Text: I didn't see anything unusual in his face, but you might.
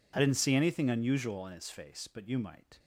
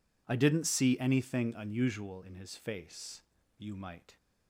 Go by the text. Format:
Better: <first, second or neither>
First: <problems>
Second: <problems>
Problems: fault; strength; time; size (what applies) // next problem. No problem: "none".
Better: first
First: none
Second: skips "but"; at 3.4 s